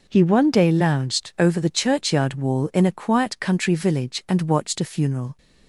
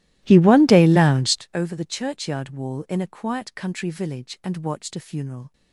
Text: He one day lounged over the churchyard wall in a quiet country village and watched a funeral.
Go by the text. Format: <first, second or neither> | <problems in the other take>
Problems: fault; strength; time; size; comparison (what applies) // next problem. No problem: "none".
first | starts louder than the rest; strong; until 1.5 s; 16 dB